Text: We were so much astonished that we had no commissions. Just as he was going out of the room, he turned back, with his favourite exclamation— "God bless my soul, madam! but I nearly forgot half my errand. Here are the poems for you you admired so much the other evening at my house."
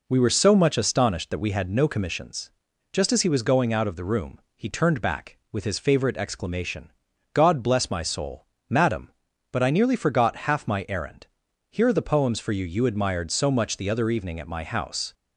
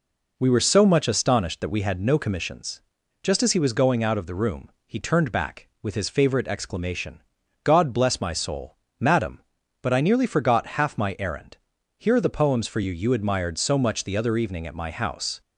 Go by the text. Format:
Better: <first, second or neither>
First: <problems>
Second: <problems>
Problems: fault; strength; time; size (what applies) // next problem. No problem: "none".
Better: neither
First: none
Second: none